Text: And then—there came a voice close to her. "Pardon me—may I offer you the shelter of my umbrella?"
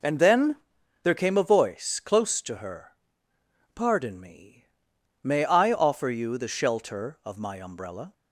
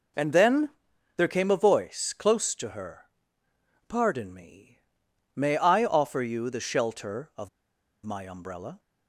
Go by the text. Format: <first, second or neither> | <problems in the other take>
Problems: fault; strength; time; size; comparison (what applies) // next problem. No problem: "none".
first | pauses between "of" and "my"; noticeable; at 7.4 s; 0.56 s long